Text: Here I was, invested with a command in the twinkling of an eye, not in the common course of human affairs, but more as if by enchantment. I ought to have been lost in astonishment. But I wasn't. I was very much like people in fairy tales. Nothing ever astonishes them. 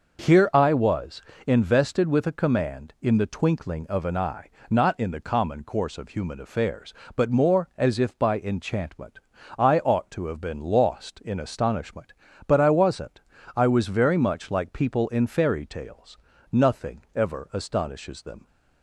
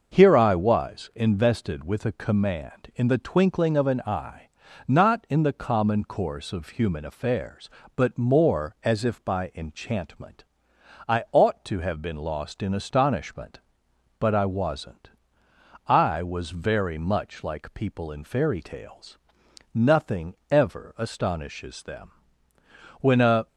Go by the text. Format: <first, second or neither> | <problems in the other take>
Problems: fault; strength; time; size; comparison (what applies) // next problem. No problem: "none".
first | starts louder than the rest; noticeable; until 1.1 s; 6 dB // pauses between "Nothing" and "ever"; slight; at 20.3 s; 0.16 s long // goes on to say "When a"; slight; from 23.0 s on; 0.46 s long